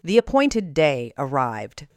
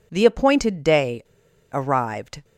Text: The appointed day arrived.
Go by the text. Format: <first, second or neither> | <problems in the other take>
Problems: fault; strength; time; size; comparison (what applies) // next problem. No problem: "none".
first | pauses between "day" and "arrived"; noticeable; at 1.2 s; 0.50 s long